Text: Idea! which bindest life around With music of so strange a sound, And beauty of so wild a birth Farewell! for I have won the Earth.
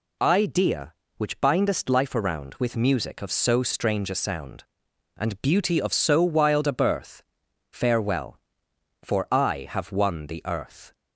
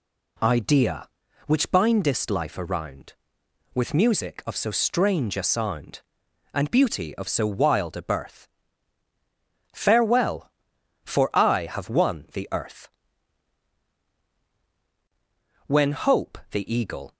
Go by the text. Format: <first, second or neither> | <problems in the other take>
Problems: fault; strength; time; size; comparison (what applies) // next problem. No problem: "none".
first | pauses between "birth" and "Farewell"; strong; at 8.4 s; 1.2 s long; noticeable in the first // goes on to say "When Hope the eagle"; from 15.6 s on; 1.4 s long